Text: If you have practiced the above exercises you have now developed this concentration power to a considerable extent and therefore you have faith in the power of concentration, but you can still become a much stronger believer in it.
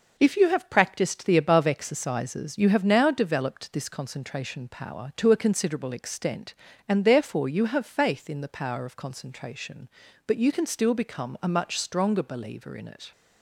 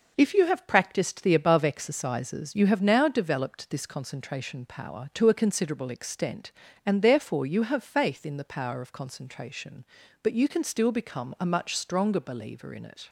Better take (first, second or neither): neither